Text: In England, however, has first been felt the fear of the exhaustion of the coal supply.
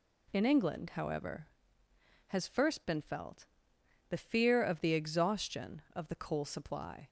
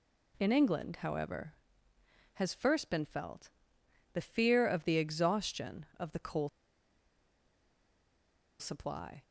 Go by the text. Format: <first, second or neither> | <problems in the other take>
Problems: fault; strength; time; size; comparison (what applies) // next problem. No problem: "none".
first | pauses between "felt" and "the"; noticeable; at 3.4 s; 0.64 s long; noticeable in the first // pauses between "coal" and "supply"; strong; at 6.4 s; 2.1 s long